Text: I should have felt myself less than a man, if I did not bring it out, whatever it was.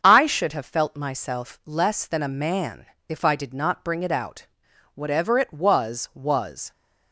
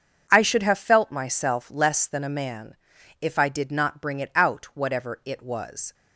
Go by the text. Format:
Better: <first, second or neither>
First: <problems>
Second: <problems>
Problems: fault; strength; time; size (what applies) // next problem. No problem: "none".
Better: second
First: starts louder than the rest; strong; until 1.0 s; 7 dB // says "was" twice; at 6.1 s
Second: starts louder than the rest; until 1.3 s; 6.5 dB